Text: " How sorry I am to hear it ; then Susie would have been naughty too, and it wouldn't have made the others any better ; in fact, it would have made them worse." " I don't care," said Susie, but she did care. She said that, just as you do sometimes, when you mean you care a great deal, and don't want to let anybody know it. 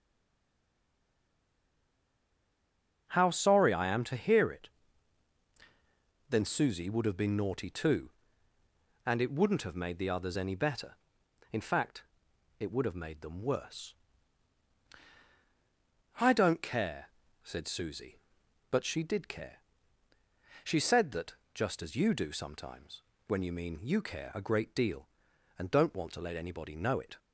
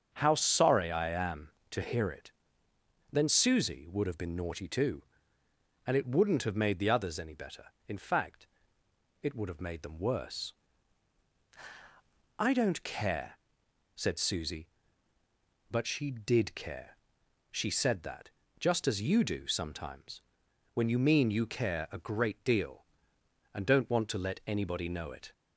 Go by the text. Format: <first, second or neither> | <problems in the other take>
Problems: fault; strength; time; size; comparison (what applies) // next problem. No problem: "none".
second | stays silent before the first word; strong; until 3.0 s; 3.0 s long // starts louder than the rest; strong; until 4.0 s; 9 dB; strong in the second